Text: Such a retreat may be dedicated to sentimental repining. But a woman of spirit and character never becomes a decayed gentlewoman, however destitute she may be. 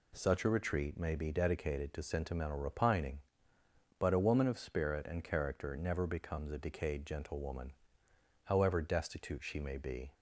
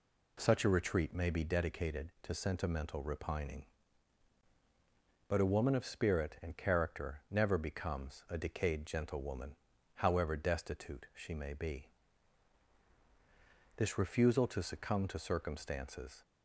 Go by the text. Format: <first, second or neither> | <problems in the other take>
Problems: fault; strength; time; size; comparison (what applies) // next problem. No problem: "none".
first | goes on to say "This refusal to succumb to circumstances"; strong; from 13.7 s on; 2.4 s long